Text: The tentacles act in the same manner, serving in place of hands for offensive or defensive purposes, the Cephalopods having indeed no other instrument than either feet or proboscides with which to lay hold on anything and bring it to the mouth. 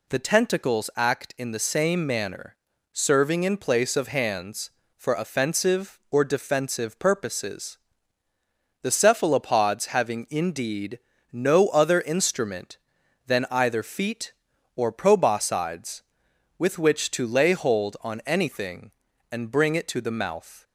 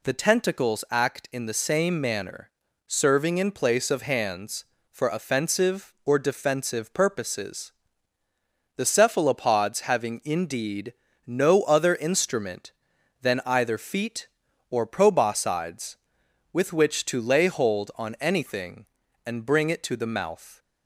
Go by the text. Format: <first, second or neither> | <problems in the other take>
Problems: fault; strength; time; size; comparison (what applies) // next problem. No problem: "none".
neither | pauses between "indeed" and "no"; slight; the same in both